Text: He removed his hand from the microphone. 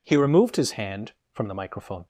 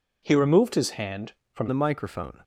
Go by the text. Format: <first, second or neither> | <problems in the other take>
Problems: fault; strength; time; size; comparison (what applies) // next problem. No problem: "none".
first | changes voice at "the"; from 1.6 s on; 0.8 s long